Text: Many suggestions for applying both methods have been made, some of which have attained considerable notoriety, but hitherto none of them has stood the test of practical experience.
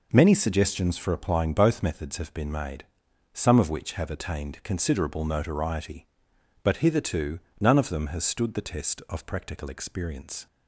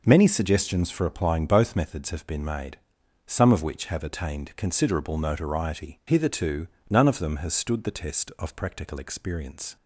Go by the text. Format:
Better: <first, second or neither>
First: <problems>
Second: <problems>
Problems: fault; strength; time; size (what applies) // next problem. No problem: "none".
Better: first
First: pauses between "hitherto" and "none"; slight; at 7.3 s; 0.18 s long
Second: skips "but"; at 6.0 s // pauses between "hitherto" and "none"; slight; at 6.6 s; 0.20 s long